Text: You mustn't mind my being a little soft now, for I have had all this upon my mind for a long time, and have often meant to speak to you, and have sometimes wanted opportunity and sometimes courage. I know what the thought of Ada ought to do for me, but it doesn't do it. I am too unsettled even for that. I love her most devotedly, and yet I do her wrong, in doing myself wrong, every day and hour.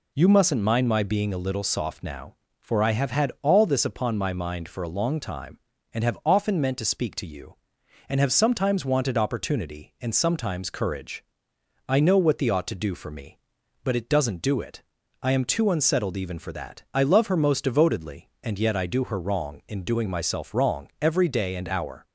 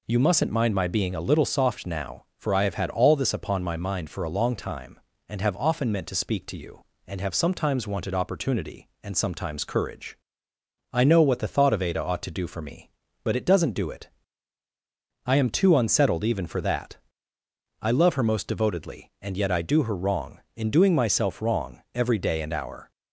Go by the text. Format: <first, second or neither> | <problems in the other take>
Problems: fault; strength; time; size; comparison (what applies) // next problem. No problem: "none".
second | skips "thought of Ada"; at 12.5 s